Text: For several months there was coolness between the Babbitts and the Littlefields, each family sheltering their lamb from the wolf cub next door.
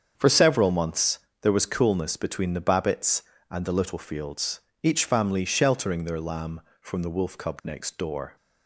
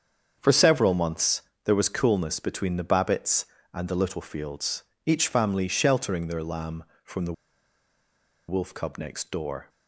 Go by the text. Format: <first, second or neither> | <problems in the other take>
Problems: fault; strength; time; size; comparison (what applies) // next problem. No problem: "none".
first | starts louder than the rest; strong; until 1.4 s; 7 dB; strong in the first // pauses between "months" and "there"; slight; at 1.4 s; 0.24 s long; slight in the first // pauses between "the" and "wolf"; at 7.3 s; 1.1 s long